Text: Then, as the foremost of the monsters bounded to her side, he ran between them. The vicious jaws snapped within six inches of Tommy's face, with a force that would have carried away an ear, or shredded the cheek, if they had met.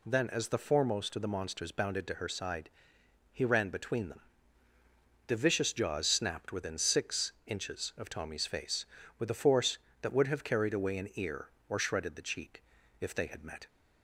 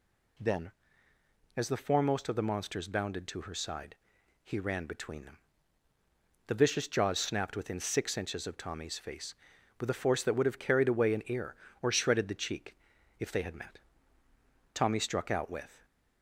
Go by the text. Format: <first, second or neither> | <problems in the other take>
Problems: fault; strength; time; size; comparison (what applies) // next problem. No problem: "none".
first | goes on to say "Tommy struck out with"; noticeable; from 14.7 s on; 1.1 s long